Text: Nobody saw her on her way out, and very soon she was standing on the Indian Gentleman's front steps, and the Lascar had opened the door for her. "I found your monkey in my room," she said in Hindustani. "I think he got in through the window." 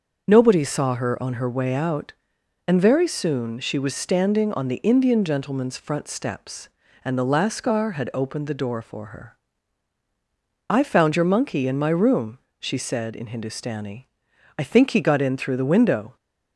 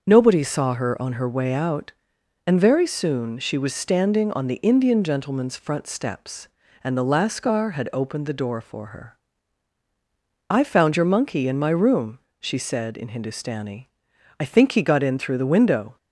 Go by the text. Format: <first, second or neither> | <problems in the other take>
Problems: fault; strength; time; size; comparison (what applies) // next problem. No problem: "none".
neither | starts louder than the rest; the same in both